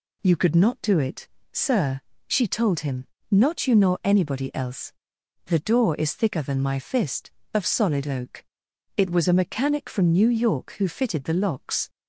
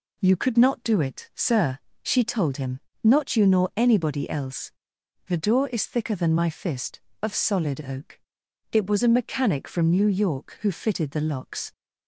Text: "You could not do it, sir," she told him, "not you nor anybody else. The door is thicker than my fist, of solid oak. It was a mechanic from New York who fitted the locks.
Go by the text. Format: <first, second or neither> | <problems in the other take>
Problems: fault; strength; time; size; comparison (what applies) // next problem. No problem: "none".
neither | none